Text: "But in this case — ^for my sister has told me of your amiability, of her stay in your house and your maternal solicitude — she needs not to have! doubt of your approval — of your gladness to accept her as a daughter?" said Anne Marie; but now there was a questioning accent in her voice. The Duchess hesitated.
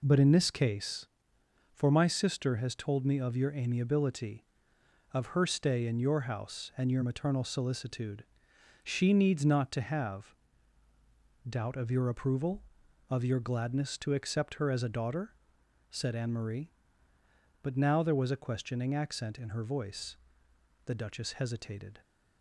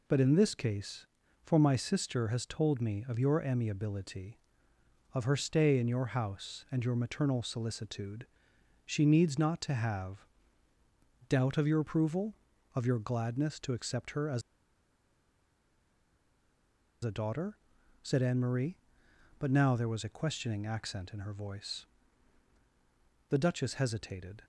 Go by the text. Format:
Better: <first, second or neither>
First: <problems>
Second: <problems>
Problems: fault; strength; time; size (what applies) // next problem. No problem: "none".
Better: first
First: none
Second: pauses between "as" and "a"; strong; at 14.4 s; 2.6 s long